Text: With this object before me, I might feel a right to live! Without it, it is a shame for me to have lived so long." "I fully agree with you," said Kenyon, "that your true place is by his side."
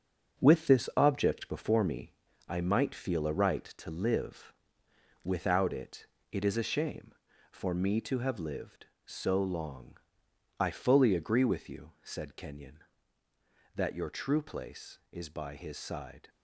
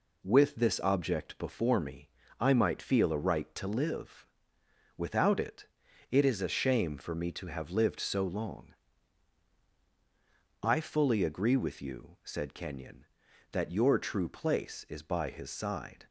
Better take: second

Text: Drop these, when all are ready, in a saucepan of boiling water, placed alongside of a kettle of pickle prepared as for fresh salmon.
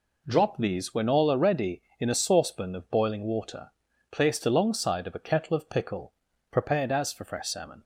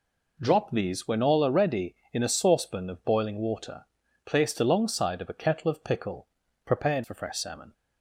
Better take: first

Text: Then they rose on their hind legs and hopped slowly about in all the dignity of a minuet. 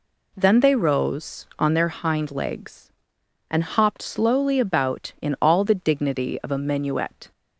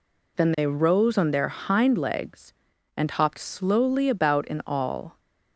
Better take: first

